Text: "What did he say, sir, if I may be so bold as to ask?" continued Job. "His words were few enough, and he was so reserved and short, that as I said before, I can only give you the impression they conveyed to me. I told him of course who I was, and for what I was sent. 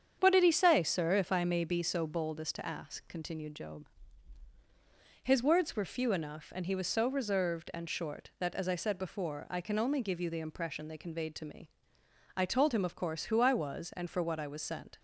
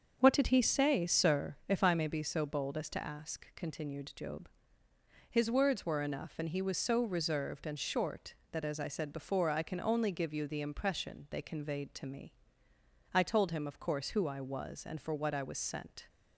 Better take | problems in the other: first | starts louder than the rest; until 1.2 s; 7 dB; strong in the first // skips "few"; at 6.0 s

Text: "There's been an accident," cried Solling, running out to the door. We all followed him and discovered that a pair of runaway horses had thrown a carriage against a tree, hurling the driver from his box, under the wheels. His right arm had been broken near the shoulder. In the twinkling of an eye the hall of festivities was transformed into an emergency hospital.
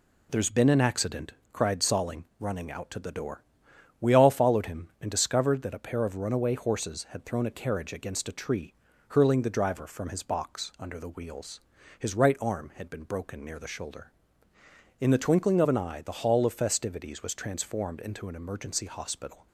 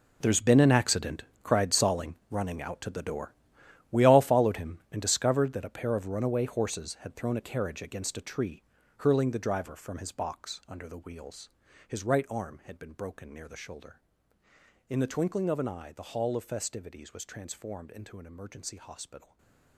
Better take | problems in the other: first | gets quieter; strong; throughout; 15 dB // stays silent after the last word; slight; from 19.1 s on; 0.6 s long

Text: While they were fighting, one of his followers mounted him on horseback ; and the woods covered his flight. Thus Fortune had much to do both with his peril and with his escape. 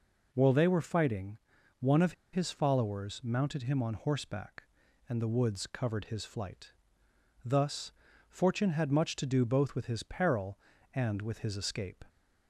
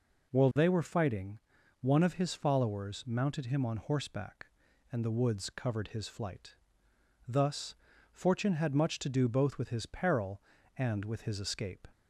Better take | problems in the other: second | pauses between "of" and "his"; slight; at 2.1 s; 0.20 s long // pauses between "Thus" and "Fortune"; at 7.9 s; 0.38 s long; also in the second

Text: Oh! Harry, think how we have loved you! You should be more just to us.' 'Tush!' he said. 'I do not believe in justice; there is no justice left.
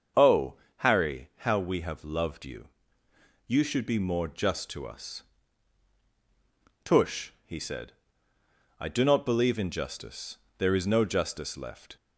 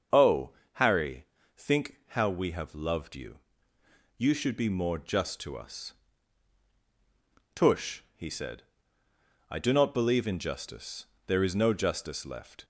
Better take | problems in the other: second | starts louder than the rest; until 1.5 s; 7 dB; also in the second // skips "think"; at 1.3 s

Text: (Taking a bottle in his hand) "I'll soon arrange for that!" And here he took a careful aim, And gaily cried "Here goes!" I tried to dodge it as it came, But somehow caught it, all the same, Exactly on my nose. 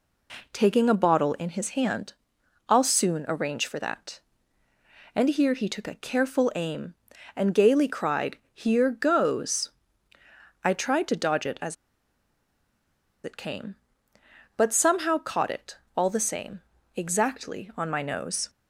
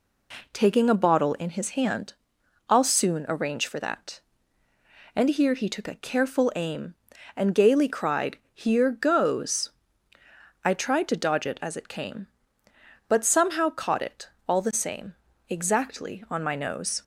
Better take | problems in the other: second | pauses between "cried" and "Here"; slight; at 8.3 s; 0.16 s long; slight in the second // pauses between "as" and "it"; strong; at 11.7 s; 1.4 s long

